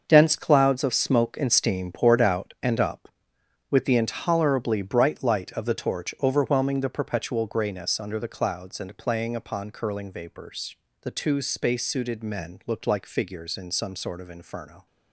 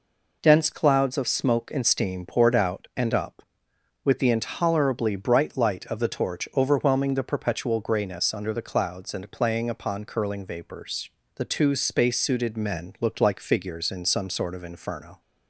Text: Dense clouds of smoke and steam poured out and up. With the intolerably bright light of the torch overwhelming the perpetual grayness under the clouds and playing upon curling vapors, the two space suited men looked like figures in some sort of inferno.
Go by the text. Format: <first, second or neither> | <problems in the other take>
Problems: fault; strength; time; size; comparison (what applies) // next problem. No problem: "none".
second | gets quieter; strong; throughout; 10.5 dB